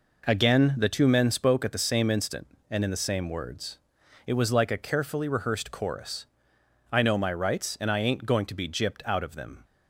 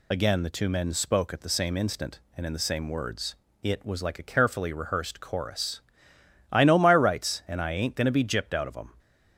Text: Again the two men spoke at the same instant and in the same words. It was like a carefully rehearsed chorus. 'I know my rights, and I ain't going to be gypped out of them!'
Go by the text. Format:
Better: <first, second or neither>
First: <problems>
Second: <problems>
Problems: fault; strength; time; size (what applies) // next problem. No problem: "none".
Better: first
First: none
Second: loses the start of "Again"; at 0.1 s; 90 ms